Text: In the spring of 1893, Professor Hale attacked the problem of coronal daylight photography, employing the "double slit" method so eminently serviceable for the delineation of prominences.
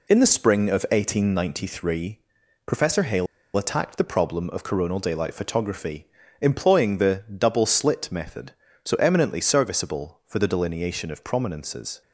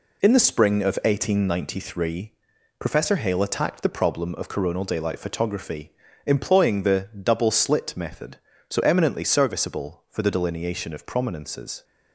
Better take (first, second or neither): second